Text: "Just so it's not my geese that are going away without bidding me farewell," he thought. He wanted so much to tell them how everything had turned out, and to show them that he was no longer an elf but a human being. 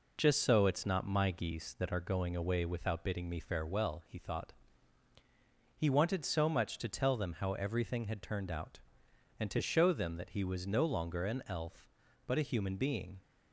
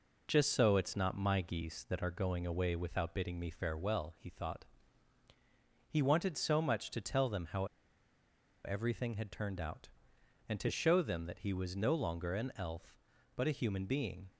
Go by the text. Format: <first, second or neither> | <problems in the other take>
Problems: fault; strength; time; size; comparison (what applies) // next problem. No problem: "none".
first | pauses between "how" and "everything"; at 7.6 s; 0.99 s long